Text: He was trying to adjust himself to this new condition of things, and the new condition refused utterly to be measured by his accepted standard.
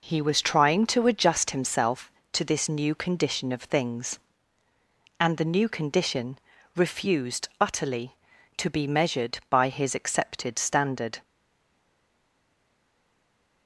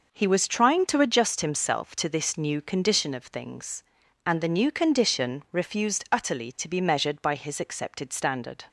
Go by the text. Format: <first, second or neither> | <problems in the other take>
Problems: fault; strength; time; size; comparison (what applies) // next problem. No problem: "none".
second | pauses between "condition" and "refused"; slight; at 6.4 s; 0.34 s long // stays silent after the last word; from 11.2 s on; 2.4 s long